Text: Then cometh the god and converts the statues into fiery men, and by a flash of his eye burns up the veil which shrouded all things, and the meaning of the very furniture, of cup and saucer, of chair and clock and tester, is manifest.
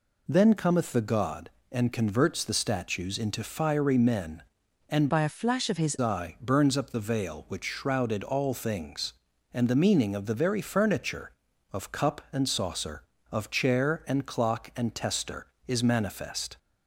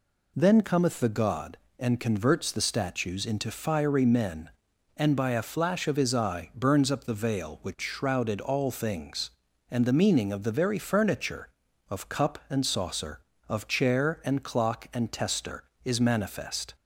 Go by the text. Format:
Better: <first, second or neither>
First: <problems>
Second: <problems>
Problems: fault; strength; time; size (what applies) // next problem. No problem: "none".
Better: second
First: changes voice from "by" to "his"; from 5.0 to 5.9 s; 0.9 s long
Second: none